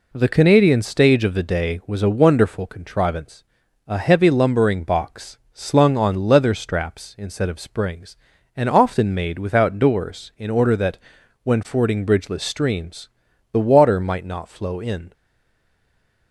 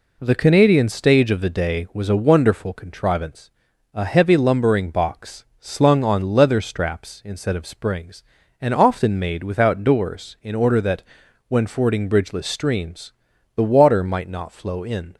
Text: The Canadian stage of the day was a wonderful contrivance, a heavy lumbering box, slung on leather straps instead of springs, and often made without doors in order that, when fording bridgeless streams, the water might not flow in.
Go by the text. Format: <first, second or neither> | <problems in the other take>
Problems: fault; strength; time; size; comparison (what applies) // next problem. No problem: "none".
second | stays silent after the last word; noticeable; from 15.1 s on; 1.2 s long